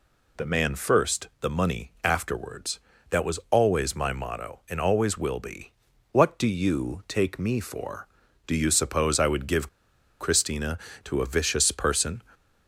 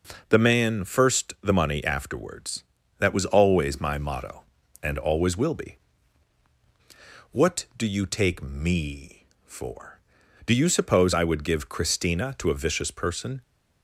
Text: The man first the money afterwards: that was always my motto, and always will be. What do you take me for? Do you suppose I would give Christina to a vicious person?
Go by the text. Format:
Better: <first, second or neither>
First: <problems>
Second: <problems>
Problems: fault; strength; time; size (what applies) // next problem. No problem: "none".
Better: second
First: pauses between "give" and "Christina"; noticeable; at 9.6 s; 0.51 s long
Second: none